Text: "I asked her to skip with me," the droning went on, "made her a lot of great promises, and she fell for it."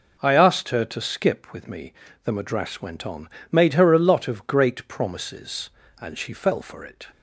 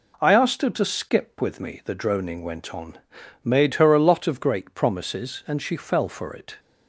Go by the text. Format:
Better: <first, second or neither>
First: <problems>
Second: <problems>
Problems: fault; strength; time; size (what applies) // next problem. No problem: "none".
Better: second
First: says "madras" for "droning"; at 2.3 s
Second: none